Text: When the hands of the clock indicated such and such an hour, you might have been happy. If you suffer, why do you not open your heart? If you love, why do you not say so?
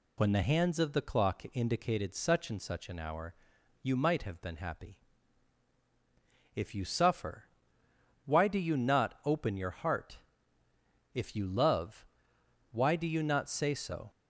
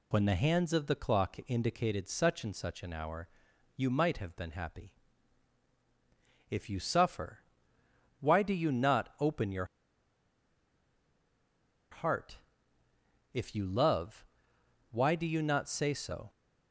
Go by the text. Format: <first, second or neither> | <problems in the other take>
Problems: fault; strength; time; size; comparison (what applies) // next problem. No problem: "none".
first | pauses between "your" and "heart"; strong; at 9.6 s; 2.2 s long